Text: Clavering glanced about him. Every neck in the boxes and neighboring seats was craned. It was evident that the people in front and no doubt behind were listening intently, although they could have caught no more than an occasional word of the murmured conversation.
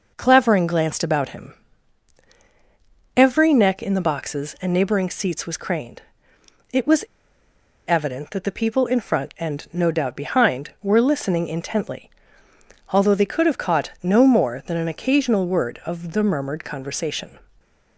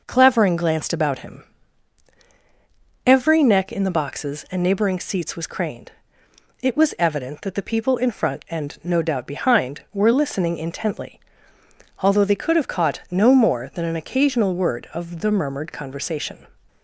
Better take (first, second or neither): second